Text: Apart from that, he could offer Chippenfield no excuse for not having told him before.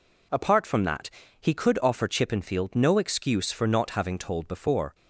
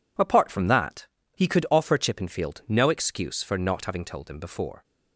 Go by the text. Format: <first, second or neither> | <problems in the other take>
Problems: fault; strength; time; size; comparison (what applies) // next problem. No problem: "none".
second | skips "him"; at 4.4 s